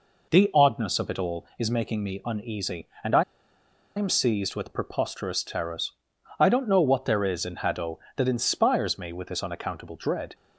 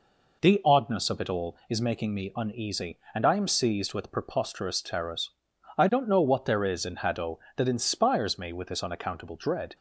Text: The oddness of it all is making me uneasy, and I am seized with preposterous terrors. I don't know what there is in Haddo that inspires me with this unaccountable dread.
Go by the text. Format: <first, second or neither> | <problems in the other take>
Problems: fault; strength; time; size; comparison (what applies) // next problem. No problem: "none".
second | pauses between "I" and "am"; noticeable; at 3.2 s; 0.75 s long